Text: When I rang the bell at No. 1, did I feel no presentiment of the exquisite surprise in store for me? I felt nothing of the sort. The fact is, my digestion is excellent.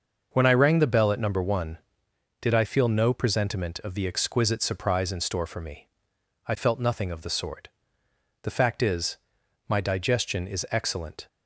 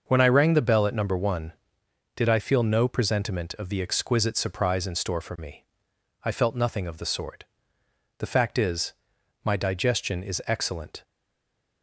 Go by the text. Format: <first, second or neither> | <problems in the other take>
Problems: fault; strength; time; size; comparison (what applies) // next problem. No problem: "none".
first | starts louder than the rest; noticeable; until 1.0 s; 6 dB; noticeable in the first // stays silent after the last word; slight; from 11.0 s on; 0.8 s long